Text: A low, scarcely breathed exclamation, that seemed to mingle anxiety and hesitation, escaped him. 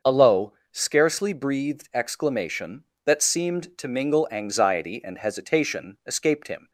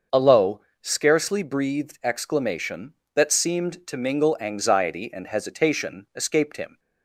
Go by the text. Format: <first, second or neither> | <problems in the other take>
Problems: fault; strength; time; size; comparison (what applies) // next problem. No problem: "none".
neither | starts louder than the rest; the same in both